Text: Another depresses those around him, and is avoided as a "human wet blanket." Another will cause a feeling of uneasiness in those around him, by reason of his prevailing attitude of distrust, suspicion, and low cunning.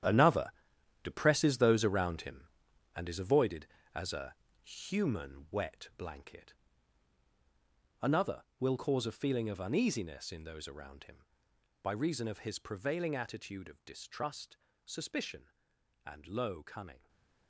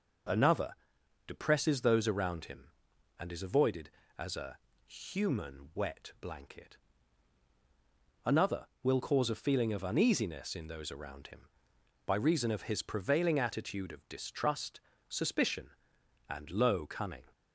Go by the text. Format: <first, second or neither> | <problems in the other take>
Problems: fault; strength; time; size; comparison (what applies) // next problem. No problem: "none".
second | gets quieter; strong; throughout; 11 dB // pauses between "Another" and "depresses"; noticeable; at 0.4 s; 0.52 s long; noticeable in the second // pauses between "a" and "human"; slight; at 4.3 s; 0.28 s long; slight in the second // stays silent after the last word; slight; from 16.9 s on; 0.5 s long